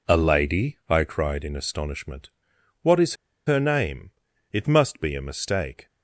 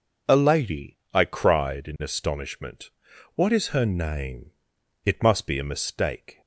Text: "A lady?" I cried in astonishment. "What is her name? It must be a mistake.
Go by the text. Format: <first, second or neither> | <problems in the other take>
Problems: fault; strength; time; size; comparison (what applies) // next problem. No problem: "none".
second | pauses between "is" and "her"; slight; at 3.1 s; 0.32 s long